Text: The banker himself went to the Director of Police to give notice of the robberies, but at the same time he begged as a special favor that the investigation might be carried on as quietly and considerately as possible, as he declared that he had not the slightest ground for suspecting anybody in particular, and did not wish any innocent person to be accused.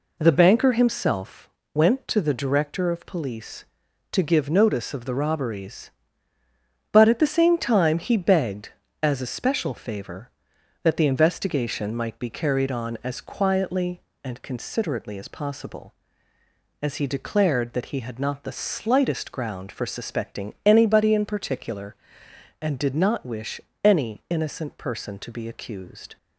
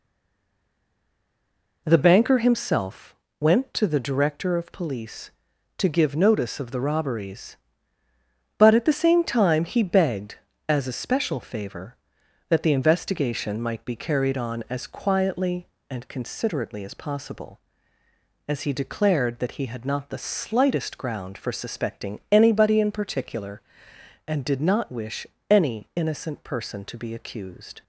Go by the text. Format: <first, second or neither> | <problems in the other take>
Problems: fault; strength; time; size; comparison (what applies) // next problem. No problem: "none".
first | stays silent before the first word; noticeable; until 1.8 s; 1.8 s long // pauses between "himself" and "went"; slight; at 3.1 s; 0.24 s long; slight in the first // pauses between "wish" and "any"; slight; at 25.2 s; 0.24 s long; slight in the first